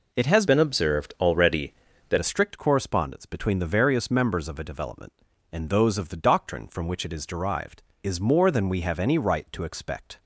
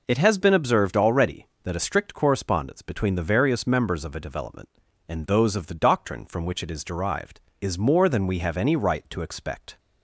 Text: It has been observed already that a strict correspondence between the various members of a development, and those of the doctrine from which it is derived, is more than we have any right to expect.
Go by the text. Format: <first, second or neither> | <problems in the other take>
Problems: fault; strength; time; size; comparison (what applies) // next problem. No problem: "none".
second | changes voice from "been" to "that"; from 0.4 to 2.1 s; 1.7 s long